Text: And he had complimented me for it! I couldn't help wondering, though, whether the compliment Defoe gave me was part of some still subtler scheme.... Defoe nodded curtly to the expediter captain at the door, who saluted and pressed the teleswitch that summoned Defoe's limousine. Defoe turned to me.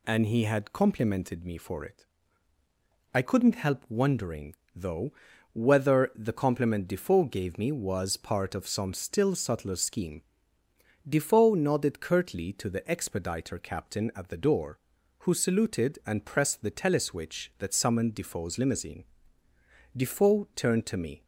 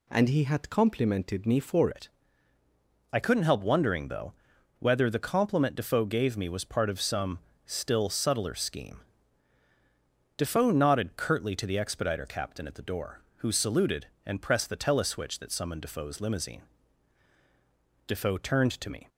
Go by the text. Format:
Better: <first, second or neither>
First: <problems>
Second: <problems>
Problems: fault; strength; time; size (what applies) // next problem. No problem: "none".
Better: first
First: none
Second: changes voice at "it"; from 1.9 s on; 17.1 s long // pauses between "some" and "still"; slight; at 7.3 s; 0.26 s long